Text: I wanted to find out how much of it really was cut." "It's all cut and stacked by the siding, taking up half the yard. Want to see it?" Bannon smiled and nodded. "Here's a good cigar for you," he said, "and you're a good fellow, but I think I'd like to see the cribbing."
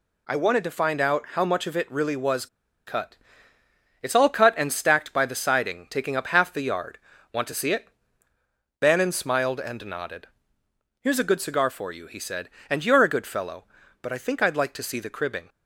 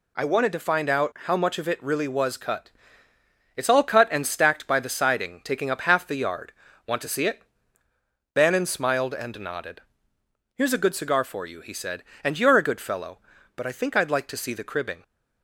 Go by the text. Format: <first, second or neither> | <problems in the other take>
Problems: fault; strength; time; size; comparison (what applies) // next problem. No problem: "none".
second | pauses between "was" and "cut"; at 2.4 s; 0.39 s long